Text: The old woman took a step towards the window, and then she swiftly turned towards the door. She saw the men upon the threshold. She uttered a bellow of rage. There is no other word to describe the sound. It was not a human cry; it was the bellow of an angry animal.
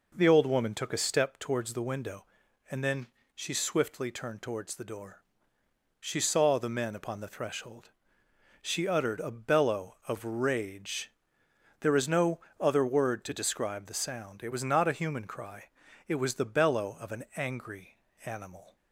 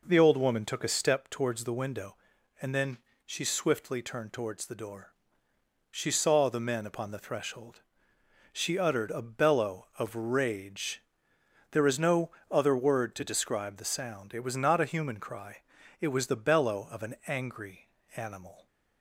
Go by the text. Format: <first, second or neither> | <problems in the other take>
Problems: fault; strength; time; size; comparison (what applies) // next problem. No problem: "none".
neither | pauses between "then" and "she"; slight; the same in both // pauses between "no" and "other"; slight; the same in both // pauses between "angry" and "animal"; slight; the same in both